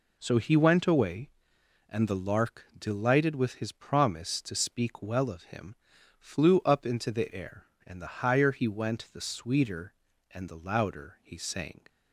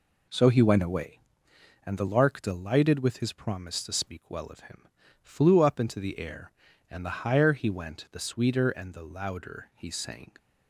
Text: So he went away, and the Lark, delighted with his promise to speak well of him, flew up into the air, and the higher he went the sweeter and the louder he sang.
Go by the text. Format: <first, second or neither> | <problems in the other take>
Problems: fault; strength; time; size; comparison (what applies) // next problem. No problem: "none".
neither | none